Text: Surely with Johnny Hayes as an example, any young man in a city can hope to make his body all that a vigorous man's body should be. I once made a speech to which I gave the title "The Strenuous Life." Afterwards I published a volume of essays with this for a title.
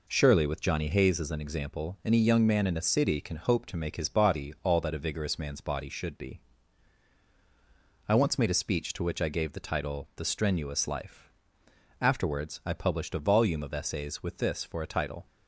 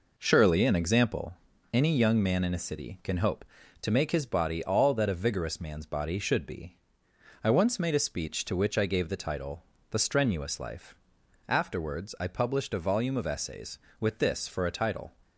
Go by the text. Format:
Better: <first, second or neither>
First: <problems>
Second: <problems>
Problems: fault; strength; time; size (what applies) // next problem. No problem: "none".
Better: first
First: none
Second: skips "with Johnny Hayes as"; at 0.6 s // pauses between "title" and "The"; slight; at 9.6 s; 0.28 s long